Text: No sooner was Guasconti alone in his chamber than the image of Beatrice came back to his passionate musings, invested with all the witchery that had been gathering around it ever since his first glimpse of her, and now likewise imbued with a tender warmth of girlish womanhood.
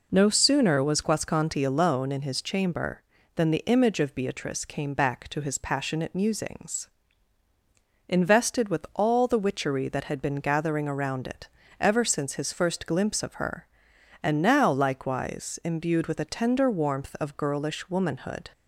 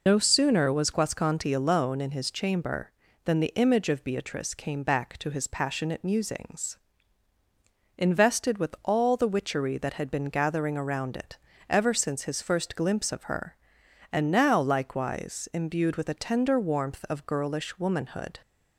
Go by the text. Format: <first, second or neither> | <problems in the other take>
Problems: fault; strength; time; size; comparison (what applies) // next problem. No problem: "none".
first | loses the start of "No"; at 0.0 s; 60 ms // pauses between "it" and "ever"; slight; at 11.3 s; 0.32 s long; slight in the first